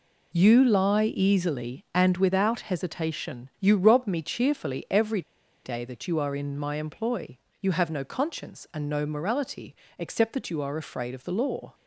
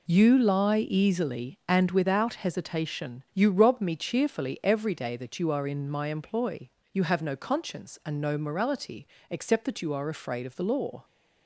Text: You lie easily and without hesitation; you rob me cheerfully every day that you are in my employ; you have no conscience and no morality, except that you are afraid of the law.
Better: second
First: pauses between "every" and "day"; at 5.2 s; 0.43 s long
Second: none

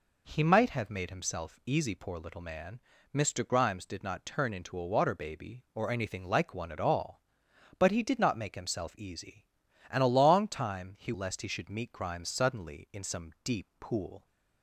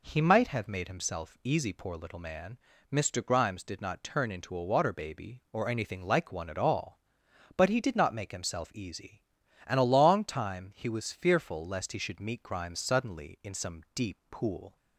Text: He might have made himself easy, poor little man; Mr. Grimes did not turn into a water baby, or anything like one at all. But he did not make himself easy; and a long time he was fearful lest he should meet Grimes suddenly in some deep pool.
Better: second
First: skips "was fearful"; at 11.1 s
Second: none

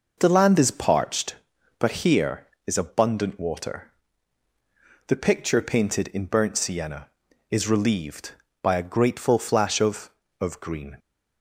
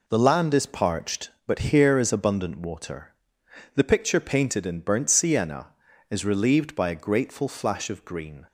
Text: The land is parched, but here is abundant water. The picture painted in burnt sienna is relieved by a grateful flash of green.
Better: second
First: says "of" twice; at 10.3 s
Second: none

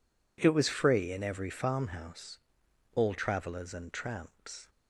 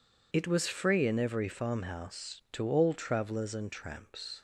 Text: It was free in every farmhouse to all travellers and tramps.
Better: second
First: skips "to"; at 2.6 s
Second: none

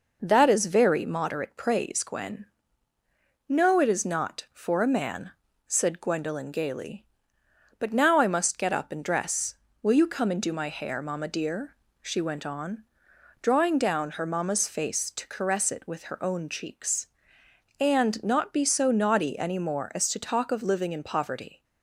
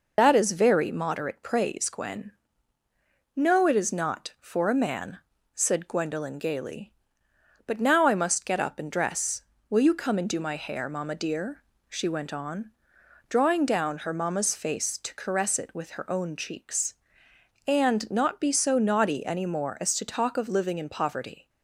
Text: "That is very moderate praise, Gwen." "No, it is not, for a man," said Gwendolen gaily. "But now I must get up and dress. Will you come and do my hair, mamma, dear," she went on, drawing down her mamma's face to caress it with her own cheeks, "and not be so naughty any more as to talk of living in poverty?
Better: first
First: none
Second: loses the start of "That"; at 0.1 s; 105 ms

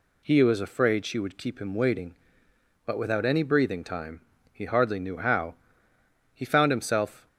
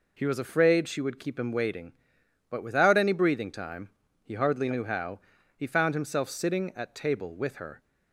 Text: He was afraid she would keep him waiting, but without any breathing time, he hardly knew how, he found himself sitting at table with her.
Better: second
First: stops before "sitting at table with her"; at 7.2 s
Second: none

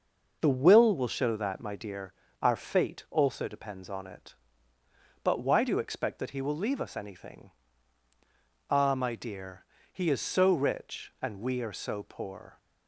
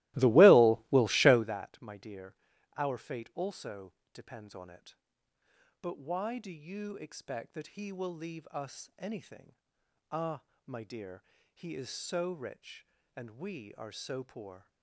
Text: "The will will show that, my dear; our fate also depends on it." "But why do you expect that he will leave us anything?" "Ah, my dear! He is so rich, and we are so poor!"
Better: first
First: none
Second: starts louder than the rest; strong; until 1.5 s; 18.5 dB // pauses between "also" and "depends"; slight; at 3.9 s; 0.22 s long

